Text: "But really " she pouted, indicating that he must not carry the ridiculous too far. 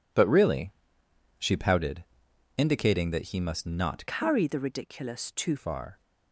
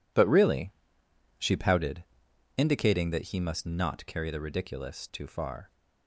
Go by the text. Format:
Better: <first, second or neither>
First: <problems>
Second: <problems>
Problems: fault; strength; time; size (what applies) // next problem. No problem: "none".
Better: second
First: changes voice from "carry" to "too"; from 4.0 to 5.5 s; 1.5 s long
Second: none